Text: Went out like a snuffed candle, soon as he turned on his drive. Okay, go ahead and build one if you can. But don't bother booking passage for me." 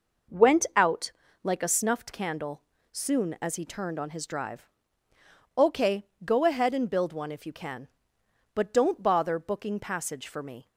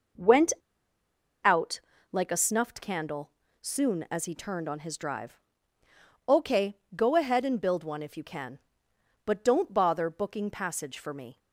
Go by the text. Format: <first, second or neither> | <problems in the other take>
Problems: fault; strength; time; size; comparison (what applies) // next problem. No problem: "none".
first | pauses between "Went" and "out"; noticeable; at 0.5 s; 0.89 s long // pauses between "out" and "like"; slight; at 1.7 s; 0.32 s long; slight in the first